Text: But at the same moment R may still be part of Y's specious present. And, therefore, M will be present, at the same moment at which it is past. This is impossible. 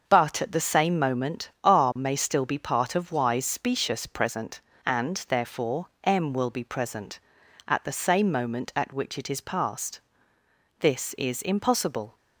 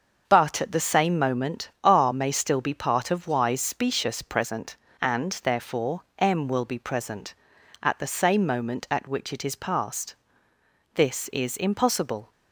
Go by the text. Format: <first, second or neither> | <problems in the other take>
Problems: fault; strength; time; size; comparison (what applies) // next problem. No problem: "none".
neither | starts louder than the rest; the same in both